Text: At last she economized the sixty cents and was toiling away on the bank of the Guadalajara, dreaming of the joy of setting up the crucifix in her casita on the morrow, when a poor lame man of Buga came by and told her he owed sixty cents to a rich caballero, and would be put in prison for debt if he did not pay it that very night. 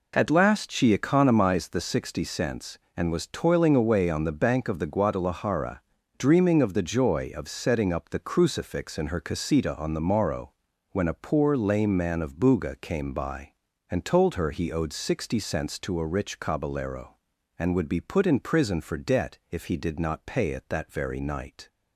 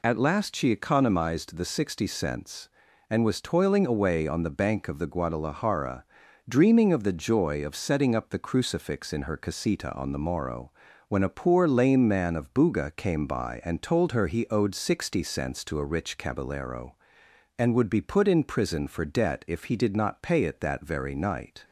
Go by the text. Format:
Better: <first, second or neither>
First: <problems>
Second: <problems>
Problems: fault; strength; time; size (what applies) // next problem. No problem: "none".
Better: neither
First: none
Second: none